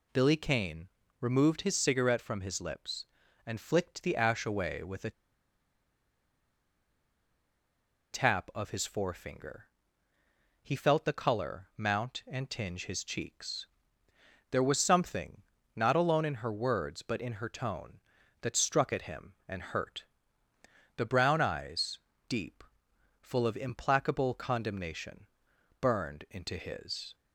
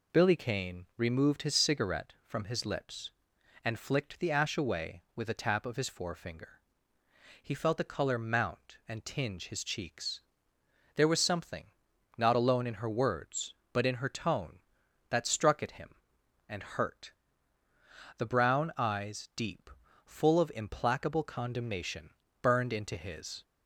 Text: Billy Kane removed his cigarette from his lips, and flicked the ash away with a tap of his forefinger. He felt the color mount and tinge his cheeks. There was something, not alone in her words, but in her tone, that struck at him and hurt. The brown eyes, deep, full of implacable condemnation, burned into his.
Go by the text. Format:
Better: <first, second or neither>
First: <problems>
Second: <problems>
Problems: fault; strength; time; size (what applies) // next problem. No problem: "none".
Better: second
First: pauses between "Kane" and "removed"; slight; at 0.8 s; 0.32 s long // pauses between "a" and "tap"; strong; at 5.1 s; 3.0 s long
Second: none